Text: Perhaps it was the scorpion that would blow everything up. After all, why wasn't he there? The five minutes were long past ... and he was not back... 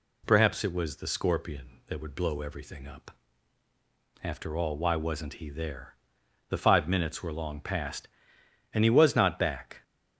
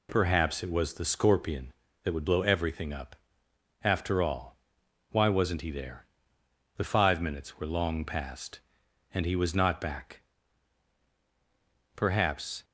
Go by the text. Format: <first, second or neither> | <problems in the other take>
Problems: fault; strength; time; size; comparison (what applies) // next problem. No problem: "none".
first | goes on to say "Perhaps"; noticeable; from 11.9 s on; 0.70 s long